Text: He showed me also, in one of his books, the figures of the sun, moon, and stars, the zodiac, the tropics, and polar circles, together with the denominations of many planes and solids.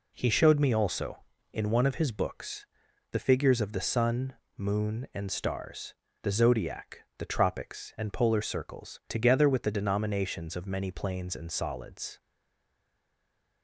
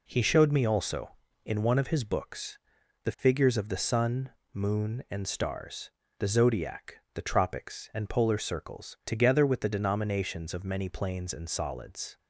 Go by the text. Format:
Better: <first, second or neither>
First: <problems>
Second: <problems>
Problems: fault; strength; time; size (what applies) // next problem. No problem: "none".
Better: second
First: stays silent after the last word; noticeable; from 12.1 s on; 1.5 s long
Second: none